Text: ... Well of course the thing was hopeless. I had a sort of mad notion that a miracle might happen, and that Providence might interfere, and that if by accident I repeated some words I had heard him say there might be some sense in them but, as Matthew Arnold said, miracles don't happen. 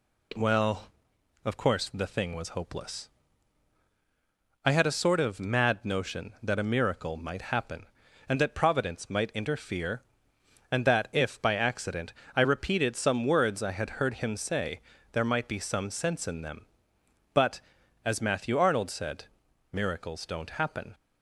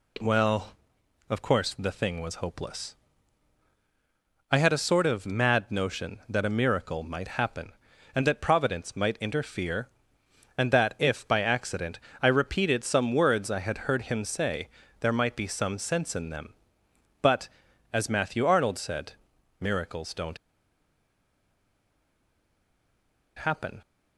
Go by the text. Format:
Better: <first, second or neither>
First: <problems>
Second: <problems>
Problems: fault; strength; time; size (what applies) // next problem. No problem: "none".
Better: first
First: pauses between "accident" and "I"; slight; at 12.1 s; 0.24 s long // pauses between "say" and "there"; slight; at 14.8 s; 0.32 s long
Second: pauses between "accident" and "I"; slight; at 11.9 s; 0.24 s long // pauses between "say" and "there"; slight; at 14.6 s; 0.32 s long // pauses between "don't" and "happen"; strong; at 20.3 s; 3.0 s long